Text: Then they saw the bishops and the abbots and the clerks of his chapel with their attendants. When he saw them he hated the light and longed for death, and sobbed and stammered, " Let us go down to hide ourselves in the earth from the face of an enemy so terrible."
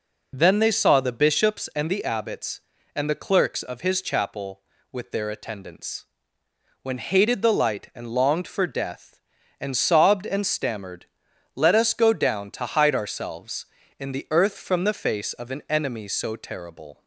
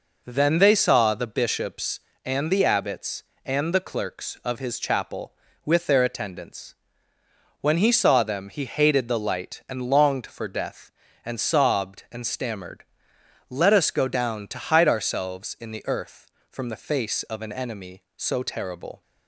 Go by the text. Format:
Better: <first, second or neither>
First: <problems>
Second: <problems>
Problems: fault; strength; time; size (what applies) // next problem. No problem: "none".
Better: second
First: skips "he saw them he"; at 6.9 s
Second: none